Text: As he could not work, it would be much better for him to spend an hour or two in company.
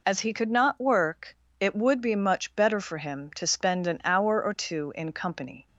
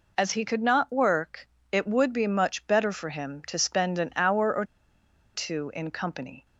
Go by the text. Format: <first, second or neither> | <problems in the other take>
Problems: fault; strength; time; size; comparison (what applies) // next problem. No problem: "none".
first | pauses between "or" and "two"; noticeable; at 4.6 s; 0.71 s long